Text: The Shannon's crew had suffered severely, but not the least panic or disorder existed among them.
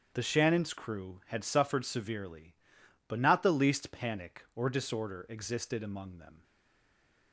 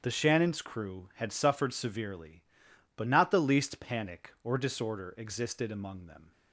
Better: second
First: starts louder than the rest; strong; until 1.1 s; 8 dB // stays silent after the last word; slight; from 6.4 s on; 0.9 s long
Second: starts louder than the rest; strong; until 1.0 s; 8 dB

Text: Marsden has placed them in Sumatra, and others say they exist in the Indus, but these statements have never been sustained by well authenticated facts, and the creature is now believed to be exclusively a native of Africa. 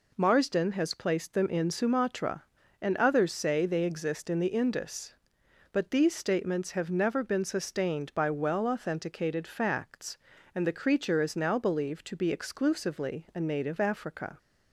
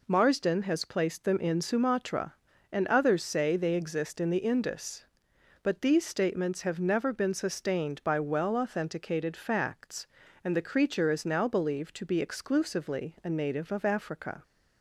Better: second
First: skips "of"; at 13.7 s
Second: none

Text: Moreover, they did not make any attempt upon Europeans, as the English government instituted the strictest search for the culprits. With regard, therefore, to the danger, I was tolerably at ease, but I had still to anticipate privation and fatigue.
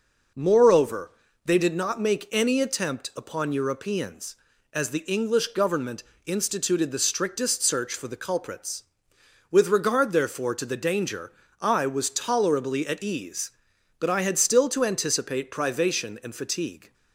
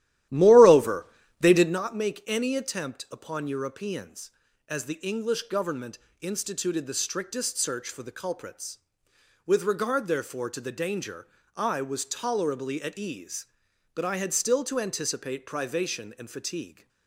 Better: first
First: pauses between "government" and "instituted"; slight; at 6.0 s; 0.22 s long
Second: starts louder than the rest; strong; until 1.9 s; 13.5 dB // pauses between "government" and "instituted"; slight; at 5.9 s; 0.22 s long

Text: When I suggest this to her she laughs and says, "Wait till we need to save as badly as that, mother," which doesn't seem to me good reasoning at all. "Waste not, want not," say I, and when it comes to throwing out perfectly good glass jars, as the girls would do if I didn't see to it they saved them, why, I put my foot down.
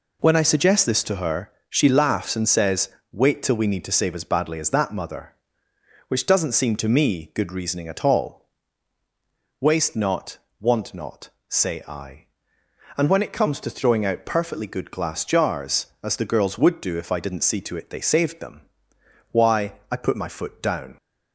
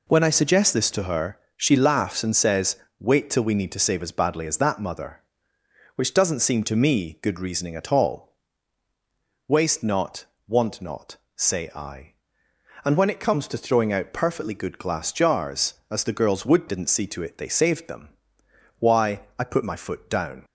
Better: first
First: pauses between "her" and "she"; slight; at 1.5 s; 0.16 s long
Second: pauses between "her" and "she"; slight; at 1.3 s; 0.16 s long // skips "do if I"; at 16.6 s

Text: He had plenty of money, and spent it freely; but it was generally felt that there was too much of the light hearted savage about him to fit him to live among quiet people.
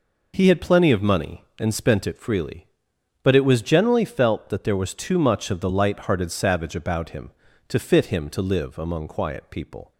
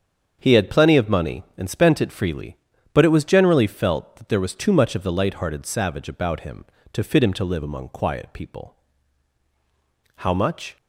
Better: first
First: none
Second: starts louder than the rest; strong; until 1.4 s; 7.5 dB // goes on to say "How much"; from 10.1 s on; 0.58 s long

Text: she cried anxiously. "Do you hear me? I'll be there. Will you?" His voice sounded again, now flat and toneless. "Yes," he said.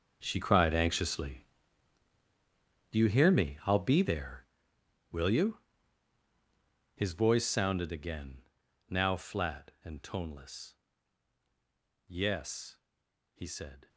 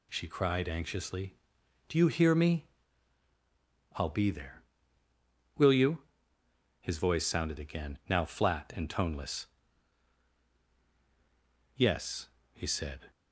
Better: second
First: gets quieter; strong; throughout; 16 dB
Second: none

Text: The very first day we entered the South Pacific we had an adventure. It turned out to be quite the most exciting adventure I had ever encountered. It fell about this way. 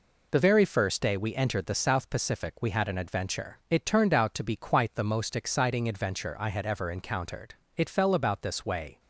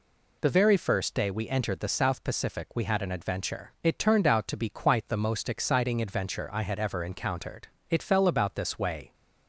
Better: second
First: gets quieter; noticeable; throughout; 6 dB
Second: none

